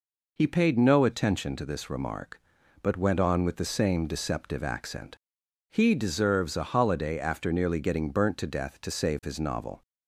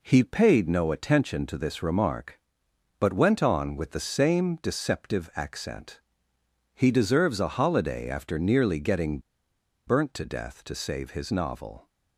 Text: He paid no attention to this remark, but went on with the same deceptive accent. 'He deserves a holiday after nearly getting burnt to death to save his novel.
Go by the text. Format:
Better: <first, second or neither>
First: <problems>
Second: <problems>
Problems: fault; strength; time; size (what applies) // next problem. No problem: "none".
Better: first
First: none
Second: pauses between "getting" and "burnt"; noticeable; at 9.1 s; 0.66 s long